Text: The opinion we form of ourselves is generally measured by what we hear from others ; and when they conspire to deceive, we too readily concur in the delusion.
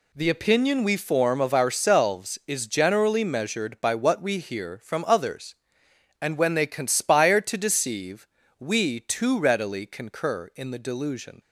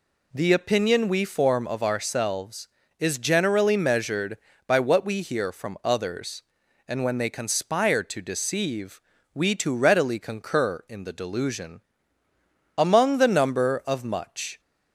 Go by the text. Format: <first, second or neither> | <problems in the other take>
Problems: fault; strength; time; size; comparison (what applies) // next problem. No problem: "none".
first | goes on to say "Among the number of much"; strong; from 12.7 s on; 1.8 s long